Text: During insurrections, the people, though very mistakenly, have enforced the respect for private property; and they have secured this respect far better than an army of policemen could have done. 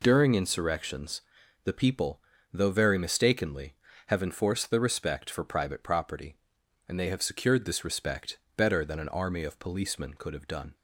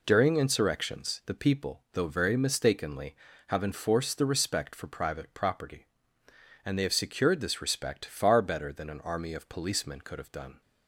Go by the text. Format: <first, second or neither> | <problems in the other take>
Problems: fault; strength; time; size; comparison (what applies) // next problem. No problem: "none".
second | skips "far"; at 8.4 s